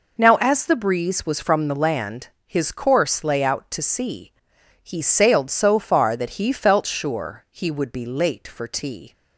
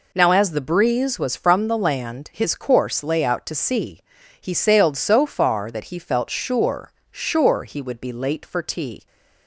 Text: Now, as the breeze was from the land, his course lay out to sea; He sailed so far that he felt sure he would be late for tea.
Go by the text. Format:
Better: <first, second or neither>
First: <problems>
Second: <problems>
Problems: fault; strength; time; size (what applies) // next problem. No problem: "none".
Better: first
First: none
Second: says "sure" twice; at 7.1 s